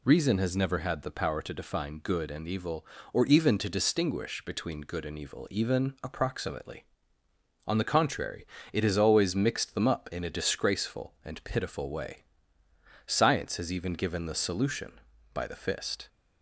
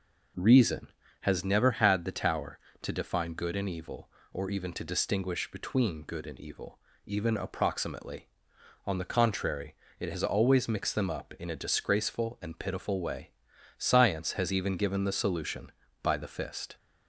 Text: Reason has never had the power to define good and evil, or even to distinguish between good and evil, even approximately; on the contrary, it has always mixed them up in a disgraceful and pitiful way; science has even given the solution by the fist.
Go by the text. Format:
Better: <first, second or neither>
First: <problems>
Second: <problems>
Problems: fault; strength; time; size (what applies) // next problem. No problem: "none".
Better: first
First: none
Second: says "tower" for "power"; at 2.1 s